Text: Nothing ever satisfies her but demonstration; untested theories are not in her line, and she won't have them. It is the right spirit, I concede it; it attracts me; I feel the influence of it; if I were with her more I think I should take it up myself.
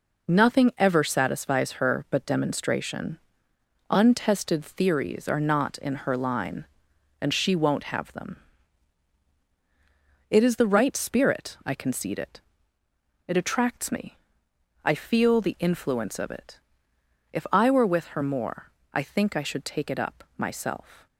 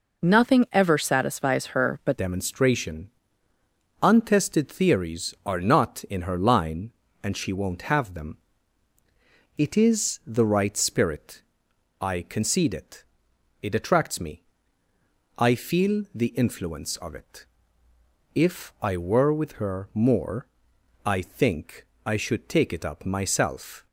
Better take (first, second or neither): first